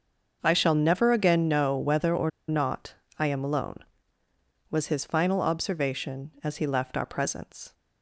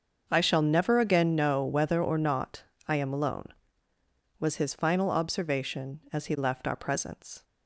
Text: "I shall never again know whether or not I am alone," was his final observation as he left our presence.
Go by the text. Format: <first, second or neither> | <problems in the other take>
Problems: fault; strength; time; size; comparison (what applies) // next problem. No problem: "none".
second | starts louder than the rest; until 1.4 s; 6.5 dB; also in the second // pauses between "or" and "not"; slight; at 2.2 s; 0.18 s long // pauses between "not" and "I"; slight; at 2.9 s; 0.22 s long; slight in the second